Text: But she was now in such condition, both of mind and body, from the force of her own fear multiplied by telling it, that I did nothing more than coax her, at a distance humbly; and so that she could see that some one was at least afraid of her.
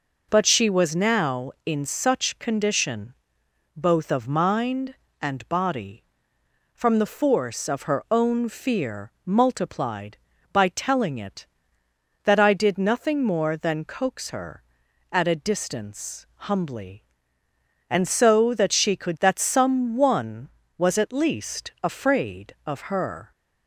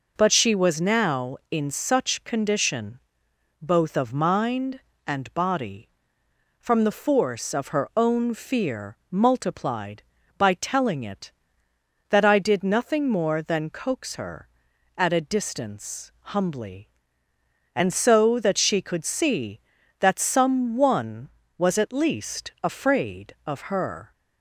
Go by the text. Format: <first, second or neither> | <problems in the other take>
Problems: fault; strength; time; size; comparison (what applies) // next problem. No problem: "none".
second | skips "see"; at 19.1 s